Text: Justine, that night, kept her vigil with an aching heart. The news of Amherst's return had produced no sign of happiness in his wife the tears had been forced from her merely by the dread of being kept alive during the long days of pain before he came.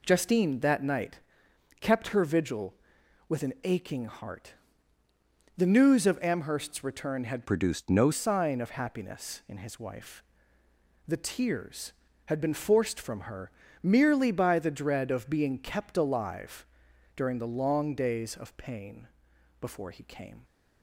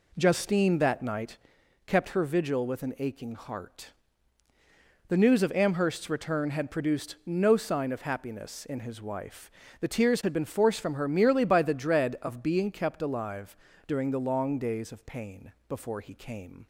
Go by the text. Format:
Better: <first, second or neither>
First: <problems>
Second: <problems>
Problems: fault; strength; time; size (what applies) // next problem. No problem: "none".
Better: second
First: changes voice from "produced" to "no"; from 7.4 to 8.1 s; 0.7 s long // pauses between "wife" and "the"; noticeable; at 10.2 s; 0.82 s long // pauses between "her" and "merely"; slight; at 13.5 s; 0.32 s long // pauses between "alive" and "during"; noticeable; at 16.6 s; 0.52 s long // pauses between "pain" and "before"; noticeable; at 19.0 s; 0.50 s long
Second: pauses between "wife" and "the"; slight; at 9.5 s; 0.28 s long // pauses between "alive" and "during"; slight; at 13.5 s; 0.32 s long // pauses between "pain" and "before"; slight; at 15.5 s; 0.16 s long